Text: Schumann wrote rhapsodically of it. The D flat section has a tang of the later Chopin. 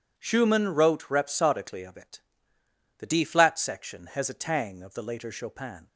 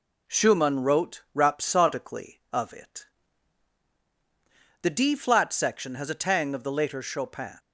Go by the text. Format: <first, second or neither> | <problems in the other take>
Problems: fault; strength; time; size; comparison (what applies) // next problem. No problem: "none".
neither | none